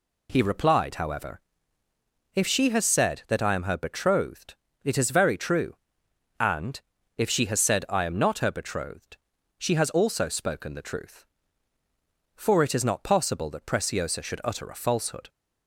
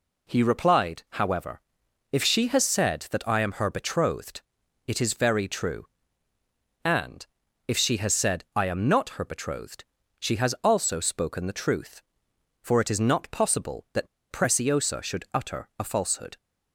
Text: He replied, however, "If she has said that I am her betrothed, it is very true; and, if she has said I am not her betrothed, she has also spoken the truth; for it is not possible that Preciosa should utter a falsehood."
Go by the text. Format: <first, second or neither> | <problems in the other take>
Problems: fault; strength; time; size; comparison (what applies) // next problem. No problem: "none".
first | pauses between "that" and "Preciosa"; slight; at 14.0 s; 0.24 s long